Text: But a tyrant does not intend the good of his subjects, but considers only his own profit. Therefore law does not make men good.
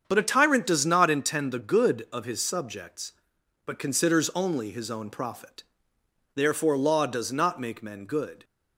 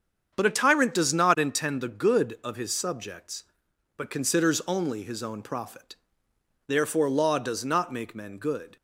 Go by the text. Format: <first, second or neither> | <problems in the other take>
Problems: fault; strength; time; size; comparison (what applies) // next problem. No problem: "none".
neither | starts louder than the rest; strong; the same in both